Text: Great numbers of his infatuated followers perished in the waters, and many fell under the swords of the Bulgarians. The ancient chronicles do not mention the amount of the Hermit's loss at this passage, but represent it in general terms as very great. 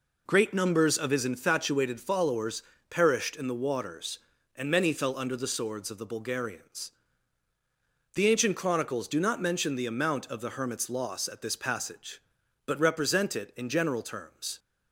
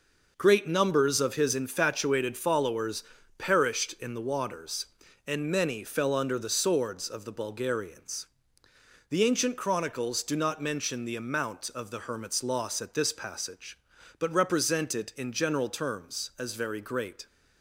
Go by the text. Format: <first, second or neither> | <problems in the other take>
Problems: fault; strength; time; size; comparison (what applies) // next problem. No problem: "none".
second | pauses between "followers" and "perished"; slight; at 2.6 s; 0.28 s long; slight in the second // stops before "as very great"; at 14.5 s